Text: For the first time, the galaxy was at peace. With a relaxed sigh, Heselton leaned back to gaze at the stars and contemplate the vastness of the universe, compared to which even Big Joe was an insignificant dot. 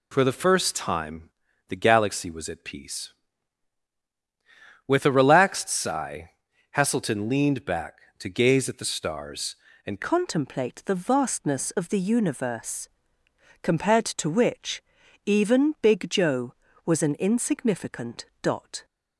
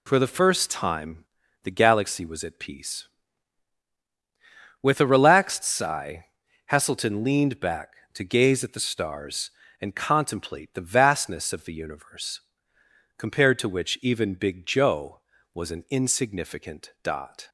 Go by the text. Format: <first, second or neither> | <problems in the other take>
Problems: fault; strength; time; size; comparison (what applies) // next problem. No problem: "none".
second | changes voice at "contemplate"; from 10.0 s on; 8.8 s long // pauses between "which" and "even"; at 14.8 s; 0.42 s long // pauses between "insignificant" and "dot"; slight; at 18.2 s; 0.18 s long